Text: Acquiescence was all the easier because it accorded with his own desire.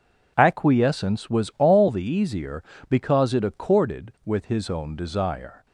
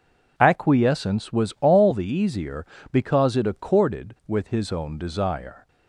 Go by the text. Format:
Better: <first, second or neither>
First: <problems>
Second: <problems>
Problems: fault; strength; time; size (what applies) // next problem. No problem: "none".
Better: neither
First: none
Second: none